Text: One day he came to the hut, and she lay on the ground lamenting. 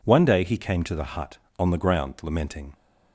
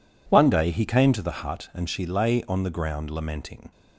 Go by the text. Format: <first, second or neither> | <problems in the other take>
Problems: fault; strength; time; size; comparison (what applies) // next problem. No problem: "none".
second | skips "and she lay"; at 1.4 s